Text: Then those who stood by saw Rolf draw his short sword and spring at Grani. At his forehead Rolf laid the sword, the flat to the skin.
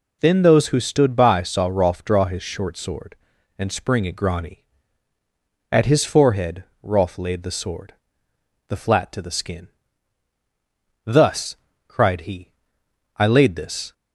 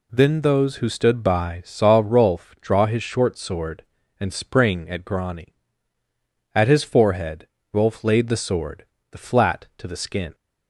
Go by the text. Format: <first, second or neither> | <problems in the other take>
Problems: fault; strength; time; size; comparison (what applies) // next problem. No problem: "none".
second | pauses between "forehead" and "Rolf"; slight; at 6.6 s; 0.18 s long; slight in the second // goes on to say "Thus cried he I laid this"; strong; from 11.0 s on; 2.8 s long